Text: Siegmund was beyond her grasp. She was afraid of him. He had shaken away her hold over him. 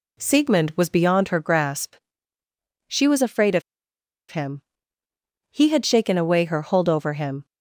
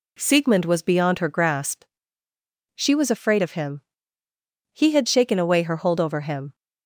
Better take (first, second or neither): second